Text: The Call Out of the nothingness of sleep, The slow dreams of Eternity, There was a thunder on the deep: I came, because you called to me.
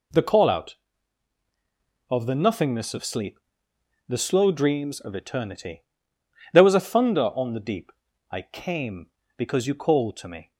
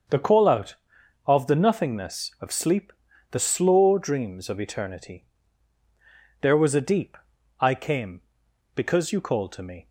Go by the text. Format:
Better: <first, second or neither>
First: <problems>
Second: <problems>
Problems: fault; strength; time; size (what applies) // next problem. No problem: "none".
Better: first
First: none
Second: starts louder than the rest; until 1.6 s; 6.5 dB // skips "thunder on the"; at 6.8 s